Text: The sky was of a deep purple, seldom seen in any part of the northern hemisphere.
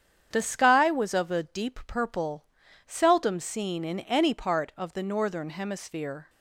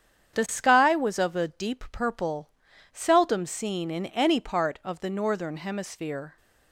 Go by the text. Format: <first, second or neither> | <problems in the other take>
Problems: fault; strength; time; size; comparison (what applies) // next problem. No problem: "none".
neither | starts louder than the rest; strong; the same in both